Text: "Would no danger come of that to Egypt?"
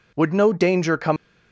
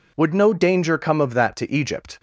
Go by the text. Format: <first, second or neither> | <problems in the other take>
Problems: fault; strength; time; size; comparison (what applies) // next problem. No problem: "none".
second | stops before "of that to Egypt"; at 1.1 s